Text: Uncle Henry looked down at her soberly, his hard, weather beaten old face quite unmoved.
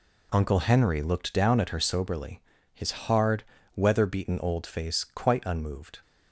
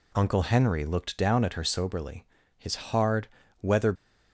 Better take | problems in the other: first | stops before "beaten old face quite unmoved"; at 3.9 s

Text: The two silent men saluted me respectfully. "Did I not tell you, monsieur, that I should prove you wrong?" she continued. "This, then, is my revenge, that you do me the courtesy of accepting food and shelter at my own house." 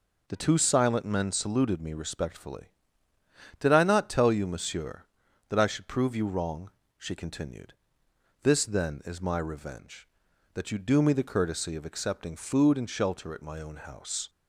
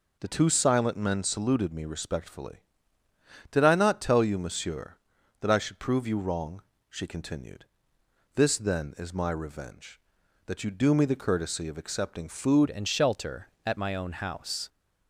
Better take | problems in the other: first | changes voice at "and"; from 12.6 s on; 2.0 s long

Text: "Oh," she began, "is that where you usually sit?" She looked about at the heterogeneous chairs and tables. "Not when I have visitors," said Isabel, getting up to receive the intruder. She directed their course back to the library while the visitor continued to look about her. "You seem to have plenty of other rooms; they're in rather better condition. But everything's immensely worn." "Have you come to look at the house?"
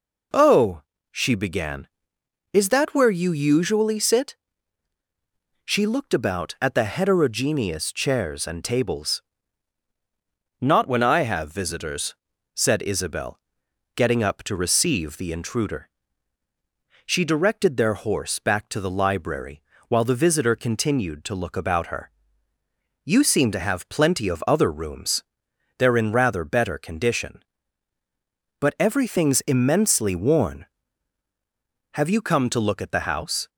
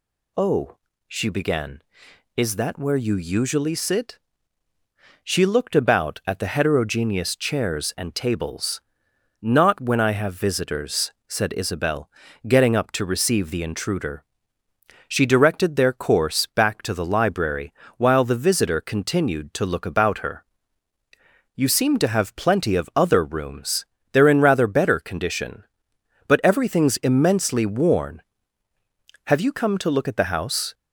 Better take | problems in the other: second | says "horse" for "course"; at 17.9 s // pauses between "library" and "while"; slight; at 19.6 s; 0.28 s long; slight in the second

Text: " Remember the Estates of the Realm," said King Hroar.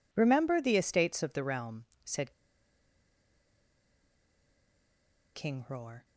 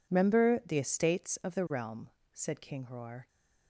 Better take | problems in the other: second | pauses between "said" and "King"; strong; at 2.3 s; 3.0 s long

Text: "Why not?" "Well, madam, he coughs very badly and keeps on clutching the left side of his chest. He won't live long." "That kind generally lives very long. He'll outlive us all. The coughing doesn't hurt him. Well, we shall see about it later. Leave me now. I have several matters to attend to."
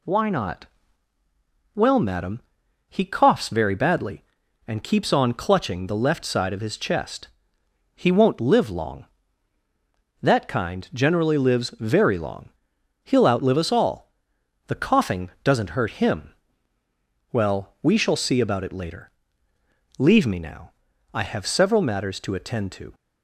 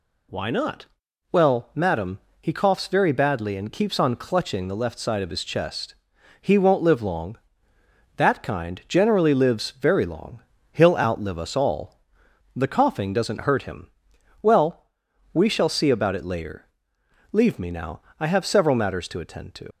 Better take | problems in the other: first | leaves "to" unfinished; at 19.7 s; 80 ms

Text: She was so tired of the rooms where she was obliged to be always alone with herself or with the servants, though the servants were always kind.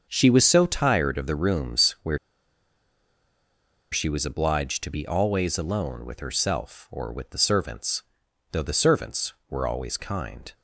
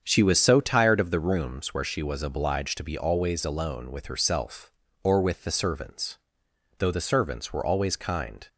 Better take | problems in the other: second | starts louder than the rest; until 1.1 s; 7 dB; strong in the second // pauses between "where" and "she"; strong; at 2.1 s; 1.7 s long

